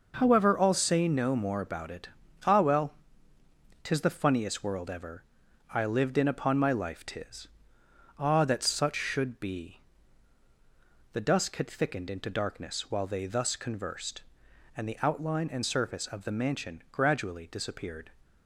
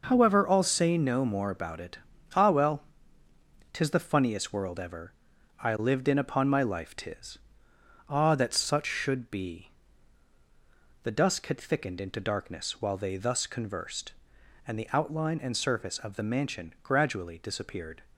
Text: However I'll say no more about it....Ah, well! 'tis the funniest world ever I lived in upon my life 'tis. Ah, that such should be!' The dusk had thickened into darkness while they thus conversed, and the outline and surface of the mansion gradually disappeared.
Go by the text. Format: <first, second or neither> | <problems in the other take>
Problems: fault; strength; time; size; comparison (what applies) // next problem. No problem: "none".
neither | pauses between "ever" and "I"; noticeable; the same in both